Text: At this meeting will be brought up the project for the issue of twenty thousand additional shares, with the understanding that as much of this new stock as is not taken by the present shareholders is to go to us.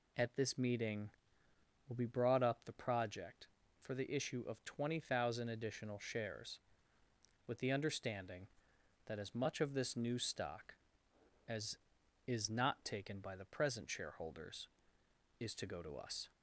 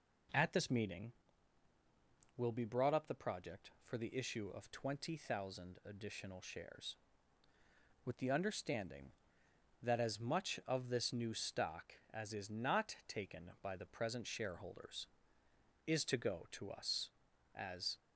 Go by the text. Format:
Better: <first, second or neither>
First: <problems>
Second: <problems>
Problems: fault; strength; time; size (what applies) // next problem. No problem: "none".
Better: first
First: none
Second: goes on to say "As"; slight; from 17.5 s on; 0.46 s long